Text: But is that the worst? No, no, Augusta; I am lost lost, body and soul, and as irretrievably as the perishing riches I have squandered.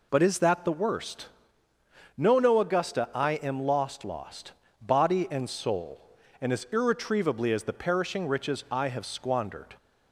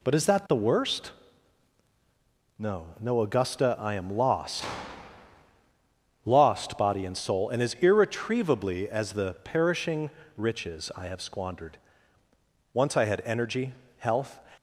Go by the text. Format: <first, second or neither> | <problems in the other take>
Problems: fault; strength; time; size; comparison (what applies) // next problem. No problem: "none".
first | pauses between "lost" and "lost"; strong; at 4.6 s; 1.6 s long // pauses between "perishing" and "riches"; slight; at 10.0 s; 0.30 s long // goes on to say "Once I had energy health"; strong; from 12.7 s on; 1.6 s long